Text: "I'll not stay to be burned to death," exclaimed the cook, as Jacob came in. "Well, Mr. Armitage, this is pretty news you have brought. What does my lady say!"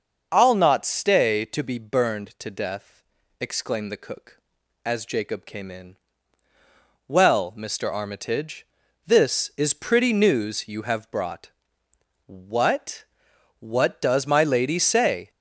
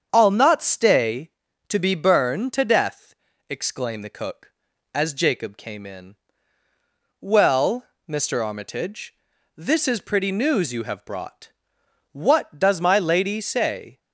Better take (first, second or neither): second